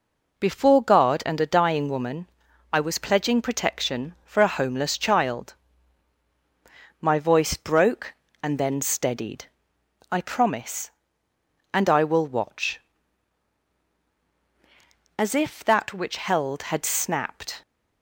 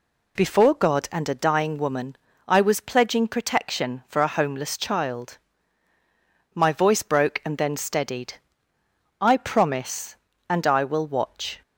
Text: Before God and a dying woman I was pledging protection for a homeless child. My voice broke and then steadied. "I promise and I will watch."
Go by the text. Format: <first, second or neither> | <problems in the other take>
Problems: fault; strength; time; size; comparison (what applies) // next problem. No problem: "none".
second | pauses between "woman" and "I"; at 2.2 s; 0.44 s long; slight in the second // goes on to say "As if that which held had snapped"; strong; from 15.1 s on; 2.4 s long